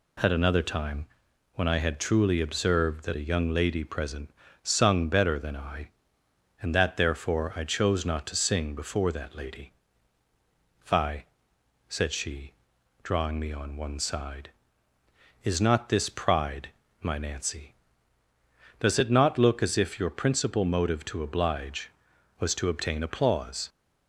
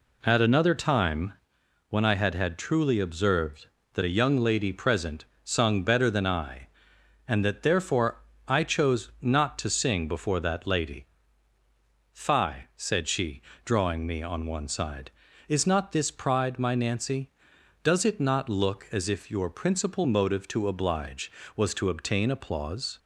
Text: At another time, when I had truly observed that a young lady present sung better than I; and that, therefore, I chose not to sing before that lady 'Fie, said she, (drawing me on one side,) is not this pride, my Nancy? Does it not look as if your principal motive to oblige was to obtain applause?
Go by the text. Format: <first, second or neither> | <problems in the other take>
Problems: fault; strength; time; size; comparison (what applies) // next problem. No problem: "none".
first | says "had" twice; at 2.3 s // pauses between "present" and "sung"; slight; at 5.2 s; 0.22 s long; slight in the first // pauses between "lady" and "Fie"; at 11.0 s; 1.0 s long; also in the first